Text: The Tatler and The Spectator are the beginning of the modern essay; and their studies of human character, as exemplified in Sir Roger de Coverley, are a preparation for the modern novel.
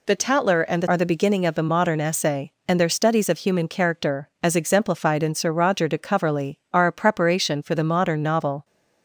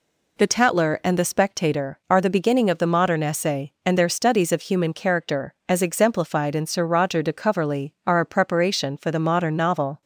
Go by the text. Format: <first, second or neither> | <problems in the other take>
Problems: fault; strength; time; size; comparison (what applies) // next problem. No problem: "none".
second | skips "Spectator"; at 0.8 s